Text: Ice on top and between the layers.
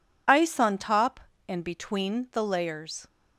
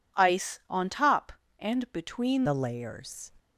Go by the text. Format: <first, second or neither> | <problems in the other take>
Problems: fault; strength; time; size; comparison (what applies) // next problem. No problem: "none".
first | changes voice at "the"; from 2.4 s on; 0.9 s long